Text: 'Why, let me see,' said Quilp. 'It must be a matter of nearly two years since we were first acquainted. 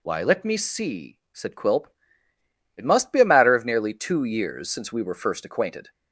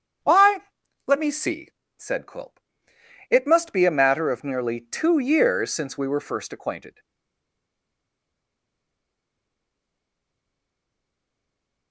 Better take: first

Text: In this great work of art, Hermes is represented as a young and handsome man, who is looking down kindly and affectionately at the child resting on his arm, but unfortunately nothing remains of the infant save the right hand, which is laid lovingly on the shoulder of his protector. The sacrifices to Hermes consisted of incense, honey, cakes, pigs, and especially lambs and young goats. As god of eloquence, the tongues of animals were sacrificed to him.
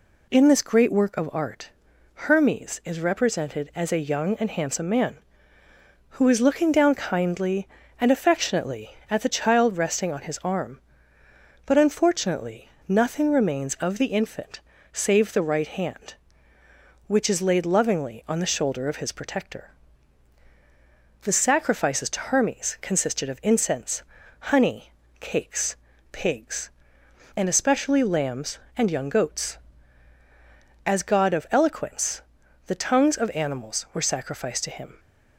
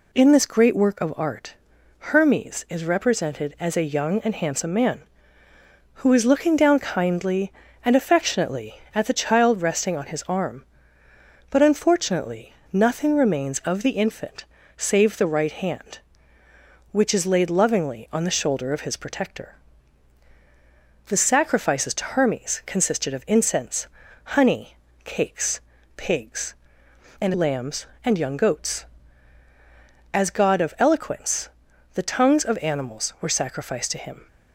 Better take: first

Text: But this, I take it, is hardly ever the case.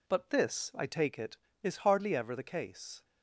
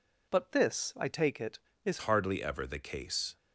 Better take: first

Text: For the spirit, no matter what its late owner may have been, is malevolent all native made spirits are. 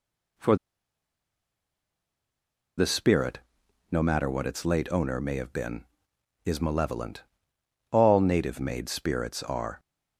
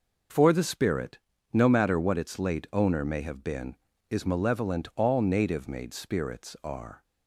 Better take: second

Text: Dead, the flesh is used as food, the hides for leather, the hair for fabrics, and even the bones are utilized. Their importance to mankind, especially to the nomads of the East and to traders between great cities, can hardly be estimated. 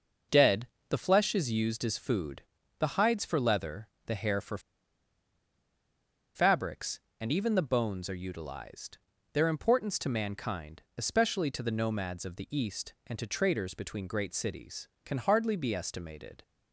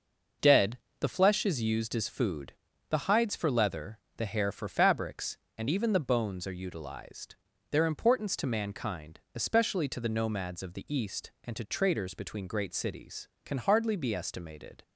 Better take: second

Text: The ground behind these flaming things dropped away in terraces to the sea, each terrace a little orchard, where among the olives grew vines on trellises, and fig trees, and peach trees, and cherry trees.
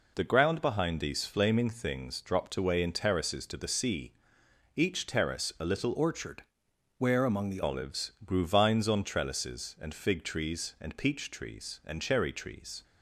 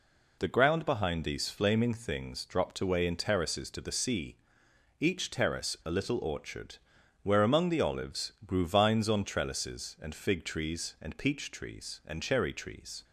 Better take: second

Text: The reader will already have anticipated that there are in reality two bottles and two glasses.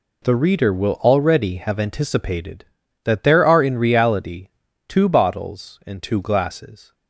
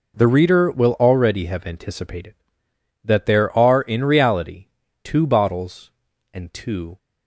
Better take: first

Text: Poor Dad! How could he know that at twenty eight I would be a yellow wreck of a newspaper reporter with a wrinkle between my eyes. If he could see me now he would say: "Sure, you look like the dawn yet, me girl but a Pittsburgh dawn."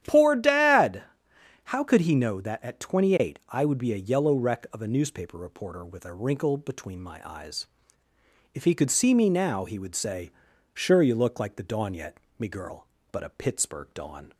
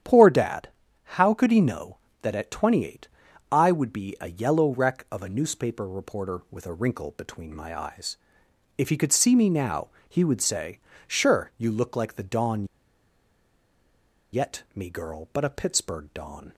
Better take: first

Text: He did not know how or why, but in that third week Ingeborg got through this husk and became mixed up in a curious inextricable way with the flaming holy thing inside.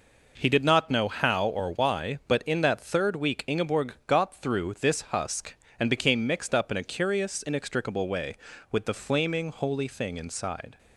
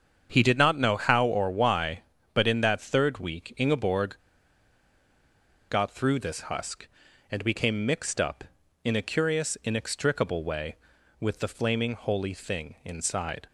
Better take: first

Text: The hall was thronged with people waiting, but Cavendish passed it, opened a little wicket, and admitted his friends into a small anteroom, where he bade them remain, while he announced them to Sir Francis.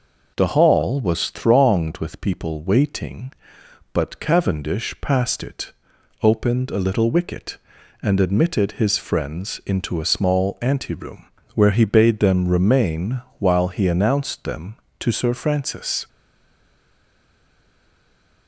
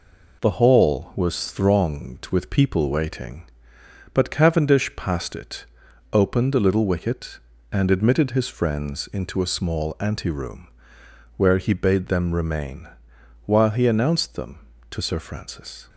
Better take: second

